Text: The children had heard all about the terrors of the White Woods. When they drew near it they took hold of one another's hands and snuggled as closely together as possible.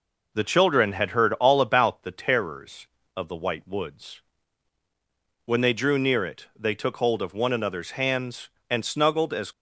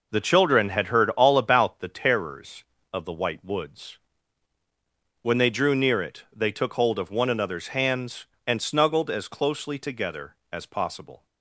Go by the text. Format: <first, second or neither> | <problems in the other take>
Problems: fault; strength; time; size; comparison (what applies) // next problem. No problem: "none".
second | stops before "closely together as possible"; at 9.5 s